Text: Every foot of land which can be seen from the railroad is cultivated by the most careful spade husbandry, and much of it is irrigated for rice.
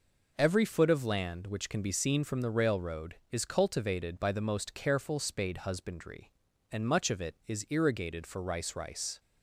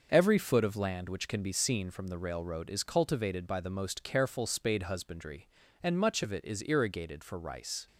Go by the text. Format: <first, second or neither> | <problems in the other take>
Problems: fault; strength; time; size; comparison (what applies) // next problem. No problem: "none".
second | says "rice" twice; at 8.7 s